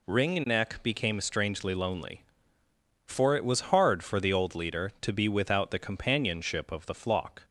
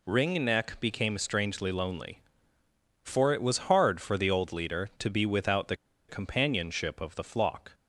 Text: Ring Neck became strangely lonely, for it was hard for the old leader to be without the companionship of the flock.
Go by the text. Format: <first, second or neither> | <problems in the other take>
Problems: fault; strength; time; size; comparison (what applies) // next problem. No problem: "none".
first | pauses between "the" and "companionship"; slight; at 5.7 s; 0.32 s long